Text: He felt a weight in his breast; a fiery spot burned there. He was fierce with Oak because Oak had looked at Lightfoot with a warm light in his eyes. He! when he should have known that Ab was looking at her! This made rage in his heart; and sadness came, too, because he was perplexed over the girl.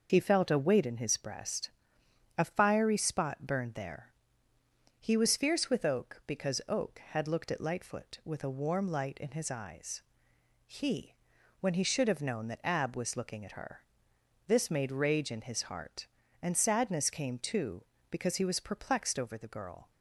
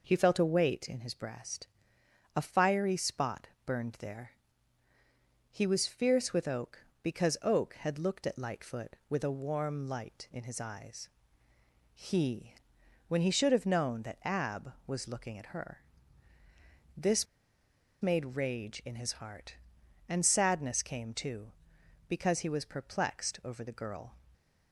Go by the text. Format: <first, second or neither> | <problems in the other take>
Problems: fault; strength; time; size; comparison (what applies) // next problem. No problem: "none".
first | pauses between "spot" and "burned"; slight; at 3.4 s; 0.18 s long // pauses between "This" and "made"; noticeable; at 17.2 s; 0.76 s long